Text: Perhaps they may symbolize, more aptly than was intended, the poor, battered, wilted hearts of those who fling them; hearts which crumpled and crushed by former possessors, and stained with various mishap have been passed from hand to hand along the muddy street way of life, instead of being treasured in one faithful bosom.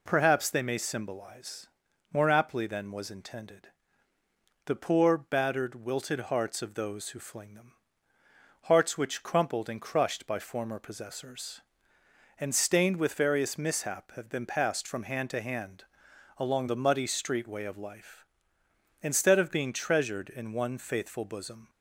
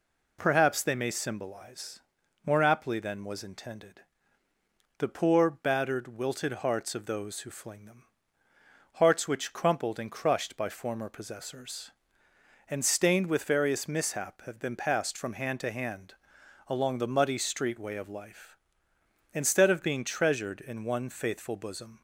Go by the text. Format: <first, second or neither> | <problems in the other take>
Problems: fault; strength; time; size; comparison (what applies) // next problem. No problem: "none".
neither | pauses between "hand" and "along"; noticeable; the same in both